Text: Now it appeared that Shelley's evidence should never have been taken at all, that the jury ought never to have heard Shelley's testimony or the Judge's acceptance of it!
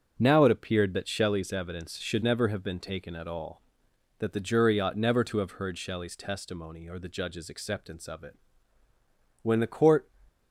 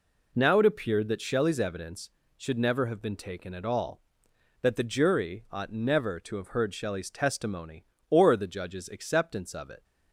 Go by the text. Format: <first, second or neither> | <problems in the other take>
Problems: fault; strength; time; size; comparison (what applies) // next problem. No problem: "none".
second | starts louder than the rest; strong; until 1.1 s; 7.5 dB // goes on to say "When the court"; noticeable; from 9.4 s on; 0.66 s long